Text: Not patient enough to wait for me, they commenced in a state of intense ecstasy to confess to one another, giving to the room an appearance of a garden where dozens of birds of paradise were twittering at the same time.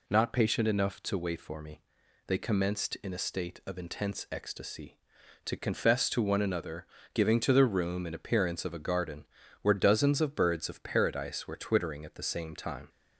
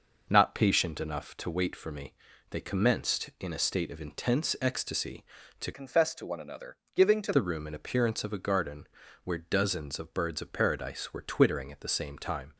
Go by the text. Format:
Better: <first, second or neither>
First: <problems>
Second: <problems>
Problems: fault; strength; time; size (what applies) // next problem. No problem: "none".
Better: first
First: pauses between "garden" and "where"; slight; at 9.2 s; 0.36 s long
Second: changes voice from "confess" to "to"; from 5.7 to 7.3 s; 1.6 s long // pauses between "garden" and "where"; slight; at 8.8 s; 0.36 s long